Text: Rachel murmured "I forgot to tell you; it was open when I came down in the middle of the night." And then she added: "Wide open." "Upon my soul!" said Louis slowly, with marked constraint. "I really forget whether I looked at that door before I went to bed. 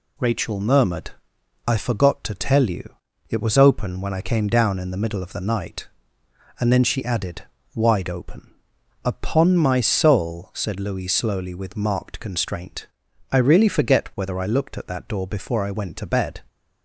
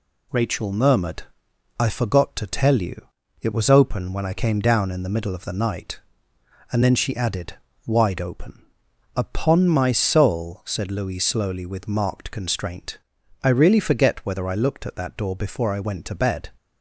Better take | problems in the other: neither | pauses between "murmured" and "I"; noticeable; the same in both

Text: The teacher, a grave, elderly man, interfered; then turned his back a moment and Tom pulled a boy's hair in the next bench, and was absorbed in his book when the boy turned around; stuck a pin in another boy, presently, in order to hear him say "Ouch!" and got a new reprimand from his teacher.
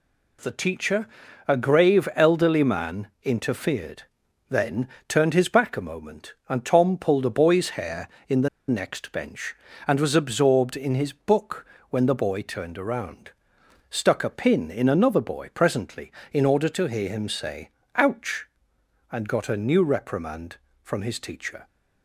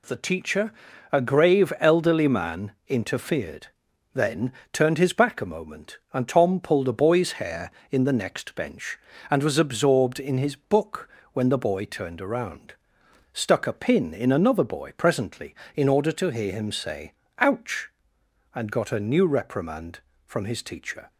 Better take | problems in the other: second | pauses between "then" and "turned"; slight; at 4.8 s; 0.22 s long; slight in the second // pauses between "the" and "next"; slight; at 8.4 s; 0.20 s long // pauses between "book" and "when"; slight; at 11.6 s; 0.26 s long; slight in the second // pauses between "say" and "Ouch"; slight; at 17.6 s; 0.26 s long; slight in the second

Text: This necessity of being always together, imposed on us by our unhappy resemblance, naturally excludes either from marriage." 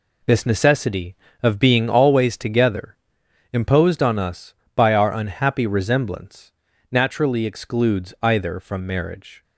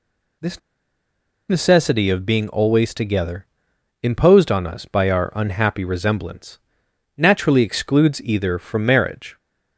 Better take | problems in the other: first | pauses between "This" and "necessity"; noticeable; at 0.5 s; 0.89 s long

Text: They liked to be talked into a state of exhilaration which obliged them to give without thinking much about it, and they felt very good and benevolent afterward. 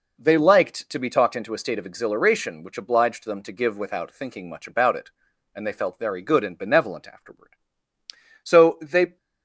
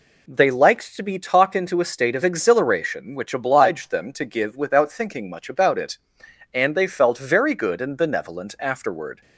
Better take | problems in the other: second | goes on to say "So they"; noticeable; from 8.4 s on; 0.74 s long

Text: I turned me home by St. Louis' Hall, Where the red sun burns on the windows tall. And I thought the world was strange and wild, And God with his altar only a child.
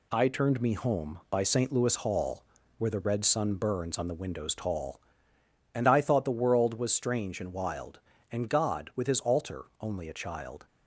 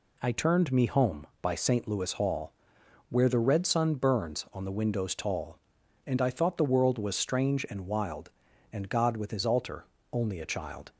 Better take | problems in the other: neither | pauses between "altar" and "only"; slight; the same in both

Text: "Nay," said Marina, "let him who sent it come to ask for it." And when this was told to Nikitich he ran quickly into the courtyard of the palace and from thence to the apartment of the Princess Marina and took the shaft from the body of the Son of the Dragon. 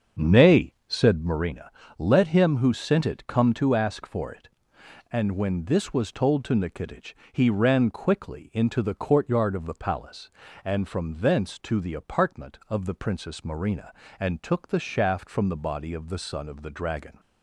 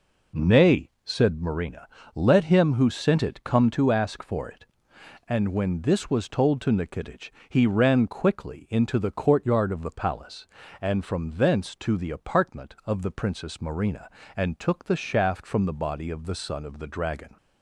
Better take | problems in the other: second | starts louder than the rest; until 1.7 s; 7 dB // pauses between "Nikitich" and "he"; slight; at 7.1 s; 0.18 s long; slight in the second

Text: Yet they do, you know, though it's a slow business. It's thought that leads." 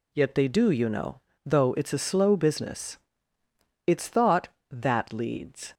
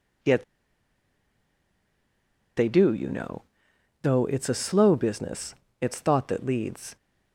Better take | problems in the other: first | pauses between "Yet" and "they"; strong; at 0.4 s; 2.1 s long

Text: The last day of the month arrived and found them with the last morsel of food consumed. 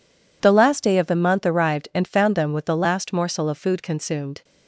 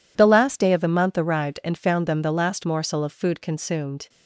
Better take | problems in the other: first | skips "with"; at 2.2 s

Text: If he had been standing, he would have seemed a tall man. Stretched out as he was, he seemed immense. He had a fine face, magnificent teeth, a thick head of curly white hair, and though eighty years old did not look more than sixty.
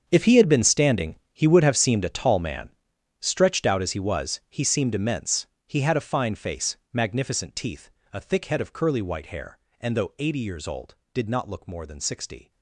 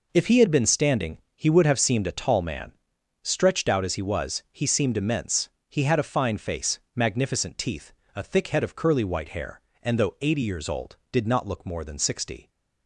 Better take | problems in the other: second | gets quieter; strong; throughout; 15 dB

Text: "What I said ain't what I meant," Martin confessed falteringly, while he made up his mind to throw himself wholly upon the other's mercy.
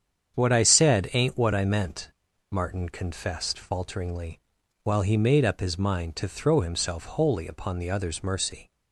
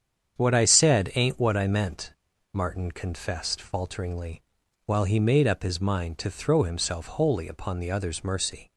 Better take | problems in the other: neither | starts louder than the rest; strong; the same in both

